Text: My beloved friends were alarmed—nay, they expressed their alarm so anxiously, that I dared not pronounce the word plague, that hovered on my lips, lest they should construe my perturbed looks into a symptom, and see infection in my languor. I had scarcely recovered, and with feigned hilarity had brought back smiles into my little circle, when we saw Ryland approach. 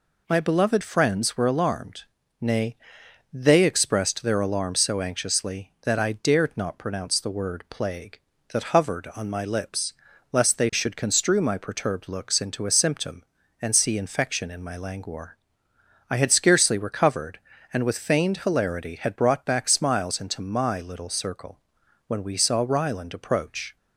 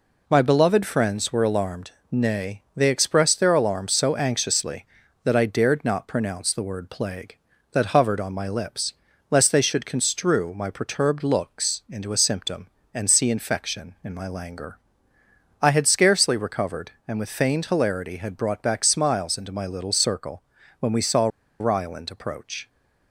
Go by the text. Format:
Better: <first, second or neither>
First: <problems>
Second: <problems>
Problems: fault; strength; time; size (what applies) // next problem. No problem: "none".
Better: first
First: none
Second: pauses between "saw" and "Ryland"; slight; at 21.2 s; 0.32 s long